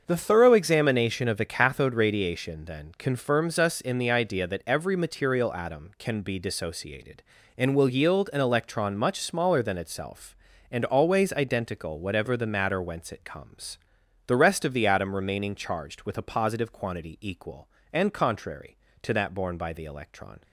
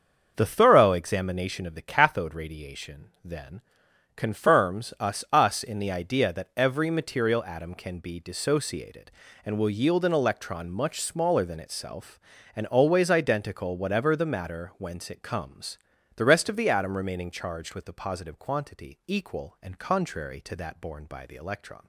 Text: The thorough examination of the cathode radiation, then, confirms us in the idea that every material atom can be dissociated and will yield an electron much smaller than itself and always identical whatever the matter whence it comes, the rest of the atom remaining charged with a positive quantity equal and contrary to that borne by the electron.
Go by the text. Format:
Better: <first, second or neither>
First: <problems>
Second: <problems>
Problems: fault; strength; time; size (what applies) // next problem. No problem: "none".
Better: first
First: starts louder than the rest; until 1.0 s; 6.5 dB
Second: starts louder than the rest; until 1.3 s; 6.5 dB // says "us" twice; at 5.3 s